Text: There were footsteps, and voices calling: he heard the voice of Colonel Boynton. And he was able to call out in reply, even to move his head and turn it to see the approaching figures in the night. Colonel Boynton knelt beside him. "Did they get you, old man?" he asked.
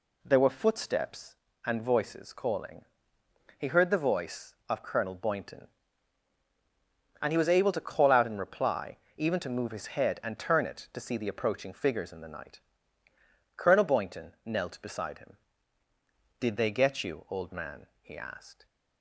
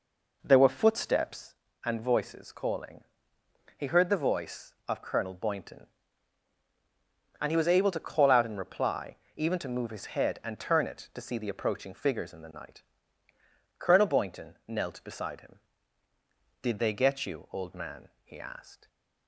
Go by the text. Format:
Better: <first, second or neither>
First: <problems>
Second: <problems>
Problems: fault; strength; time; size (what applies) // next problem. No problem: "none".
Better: first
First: none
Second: starts louder than the rest; noticeable; until 1.5 s; 4.5 dB // stays silent after the last word; slight; from 18.7 s on; 0.5 s long